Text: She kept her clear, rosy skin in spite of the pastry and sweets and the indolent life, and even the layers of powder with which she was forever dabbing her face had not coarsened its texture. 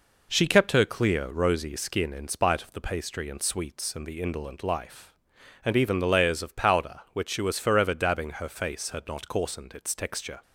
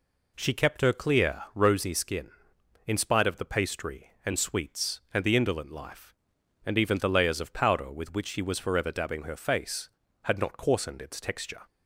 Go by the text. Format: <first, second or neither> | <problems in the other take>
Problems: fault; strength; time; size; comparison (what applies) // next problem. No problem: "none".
second | skips "with"; at 7.0 s